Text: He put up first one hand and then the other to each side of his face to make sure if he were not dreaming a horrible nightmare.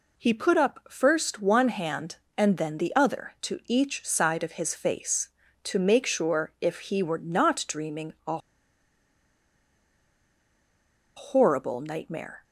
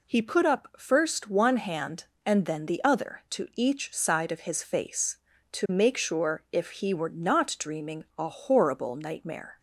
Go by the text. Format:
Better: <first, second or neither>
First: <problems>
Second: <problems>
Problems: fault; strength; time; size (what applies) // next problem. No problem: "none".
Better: second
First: pauses between "a" and "horrible"; strong; at 8.3 s; 2.7 s long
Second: none